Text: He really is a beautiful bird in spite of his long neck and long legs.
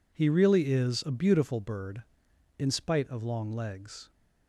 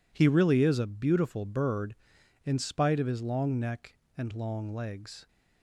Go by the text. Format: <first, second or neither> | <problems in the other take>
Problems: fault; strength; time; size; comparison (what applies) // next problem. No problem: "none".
second | skips "his long neck and"; at 3.2 s